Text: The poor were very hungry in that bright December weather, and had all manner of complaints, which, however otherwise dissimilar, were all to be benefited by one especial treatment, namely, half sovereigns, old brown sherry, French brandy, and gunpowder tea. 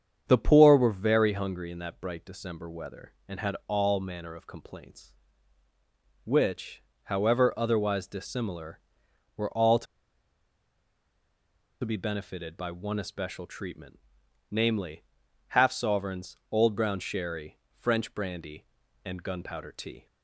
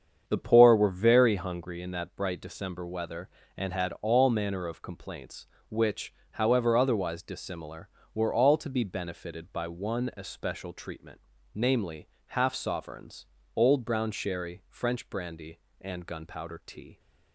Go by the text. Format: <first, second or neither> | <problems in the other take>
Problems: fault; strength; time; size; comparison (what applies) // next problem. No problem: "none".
second | starts louder than the rest; strong; until 1.2 s; 8 dB; strong in the second // pauses between "to" and "be"; strong; at 9.8 s; 1.9 s long